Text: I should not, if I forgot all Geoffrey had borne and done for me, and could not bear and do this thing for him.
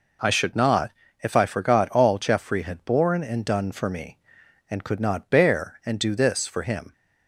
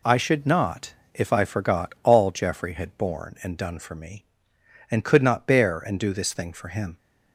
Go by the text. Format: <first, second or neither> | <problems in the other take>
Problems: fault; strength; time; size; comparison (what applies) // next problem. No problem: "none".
second | skips "thing"; at 6.4 s